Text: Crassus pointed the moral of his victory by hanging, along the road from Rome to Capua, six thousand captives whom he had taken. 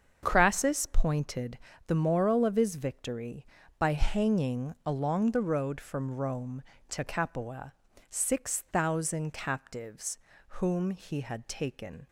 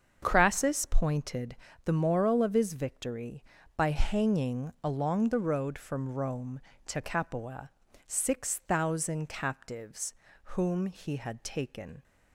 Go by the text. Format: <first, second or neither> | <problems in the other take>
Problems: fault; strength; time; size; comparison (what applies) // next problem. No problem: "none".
neither | starts louder than the rest; the same in both // pauses between "pointed" and "the"; slight; the same in both // pauses between "captives" and "whom"; the same in both